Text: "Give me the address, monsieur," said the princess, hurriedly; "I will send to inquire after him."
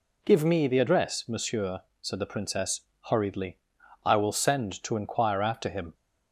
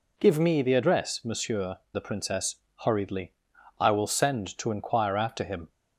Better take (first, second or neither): first